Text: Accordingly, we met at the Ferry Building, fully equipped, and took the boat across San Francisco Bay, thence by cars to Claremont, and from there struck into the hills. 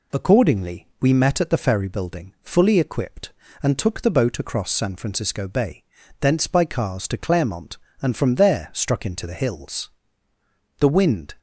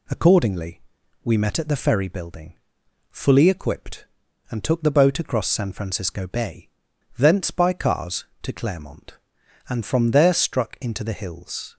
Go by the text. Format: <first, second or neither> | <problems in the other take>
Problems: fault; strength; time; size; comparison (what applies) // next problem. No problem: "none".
second | goes on to say "The wind"; from 10.7 s on; 0.56 s long